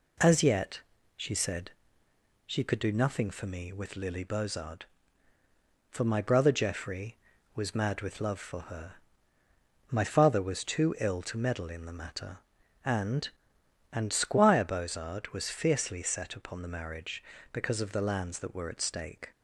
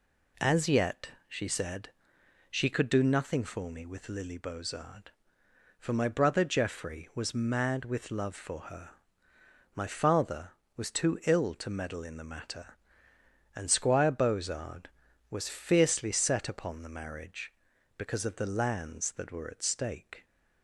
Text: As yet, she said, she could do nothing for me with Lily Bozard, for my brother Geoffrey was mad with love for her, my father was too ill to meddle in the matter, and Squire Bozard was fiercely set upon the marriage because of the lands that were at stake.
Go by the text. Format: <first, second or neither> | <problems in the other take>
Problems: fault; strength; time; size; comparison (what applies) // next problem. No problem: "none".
second | says "and" twice; at 13.9 s